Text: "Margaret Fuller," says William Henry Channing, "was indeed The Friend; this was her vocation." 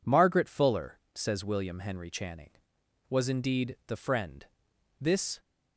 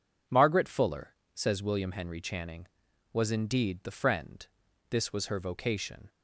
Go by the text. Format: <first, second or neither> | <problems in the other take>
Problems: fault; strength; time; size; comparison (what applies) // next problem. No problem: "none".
second | stops before "was her vocation"; at 5.3 s